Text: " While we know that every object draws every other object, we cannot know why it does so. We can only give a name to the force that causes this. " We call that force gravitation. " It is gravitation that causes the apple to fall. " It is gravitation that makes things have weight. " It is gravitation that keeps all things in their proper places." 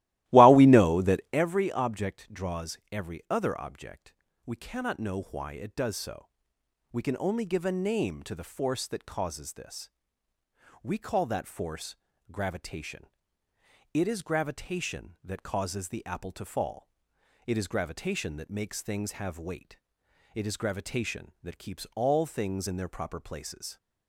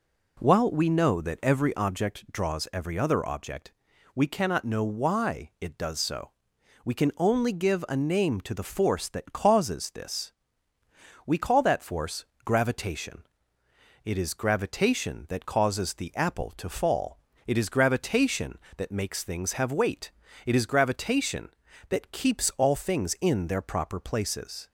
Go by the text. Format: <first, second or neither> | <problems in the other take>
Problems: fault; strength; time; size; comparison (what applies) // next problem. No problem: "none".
second | starts louder than the rest; strong; until 1.5 s; 16.5 dB // pauses between "force" and "gravitation"; slight; at 11.9 s; 0.36 s long; slight in the second